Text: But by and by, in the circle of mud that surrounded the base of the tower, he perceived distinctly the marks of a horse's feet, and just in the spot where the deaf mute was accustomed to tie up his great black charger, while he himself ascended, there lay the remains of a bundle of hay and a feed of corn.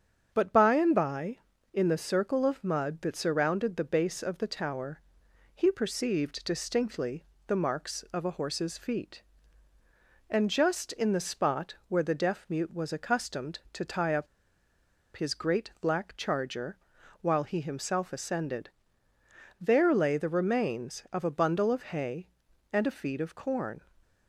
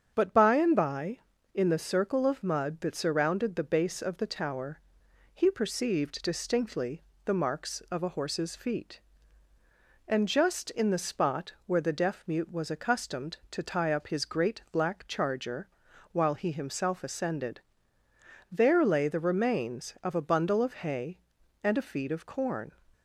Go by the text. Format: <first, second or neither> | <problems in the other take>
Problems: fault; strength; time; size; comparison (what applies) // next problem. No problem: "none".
second | starts louder than the rest; strong; until 1.3 s; 7.5 dB; strong in the second // pauses between "distinctly" and "the"; slight; at 7.2 s; 0.22 s long; slight in the second // pauses between "up" and "his"; noticeable; at 14.2 s; 0.90 s long